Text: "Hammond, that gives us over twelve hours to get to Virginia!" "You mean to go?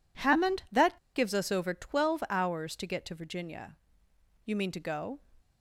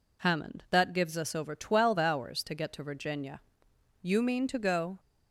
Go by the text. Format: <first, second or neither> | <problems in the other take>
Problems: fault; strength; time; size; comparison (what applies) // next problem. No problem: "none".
second | pauses between "that" and "gives"; slight; at 0.9 s; 0.19 s long